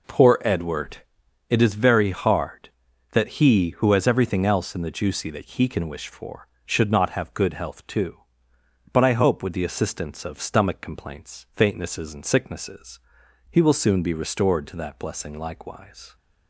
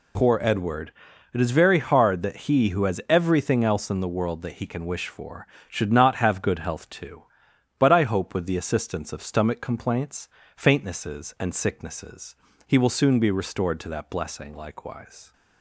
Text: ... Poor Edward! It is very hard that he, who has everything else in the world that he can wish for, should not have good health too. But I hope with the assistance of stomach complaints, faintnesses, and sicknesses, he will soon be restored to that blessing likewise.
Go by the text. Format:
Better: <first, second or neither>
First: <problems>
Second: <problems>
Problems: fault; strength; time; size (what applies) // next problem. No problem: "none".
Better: second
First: says "juicy" for "world"; at 4.9 s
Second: none